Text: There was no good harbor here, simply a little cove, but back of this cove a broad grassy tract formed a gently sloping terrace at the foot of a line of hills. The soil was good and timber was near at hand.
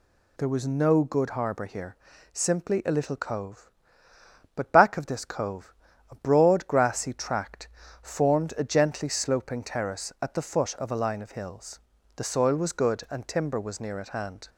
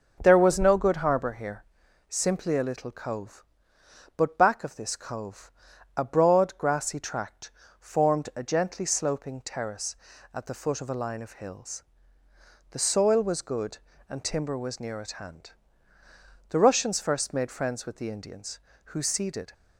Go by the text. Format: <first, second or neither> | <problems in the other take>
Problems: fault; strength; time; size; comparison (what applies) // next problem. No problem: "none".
first | pauses between "cove" and "a"; noticeable; at 5.4 s; 0.46 s long; also in the first // pauses between "tract" and "formed"; slight; at 7.5 s; 0.26 s long; slight in the first // goes on to say "The Russians first made friends with the Indians who ceded"; strong; from 16.4 s on; 3.0 s long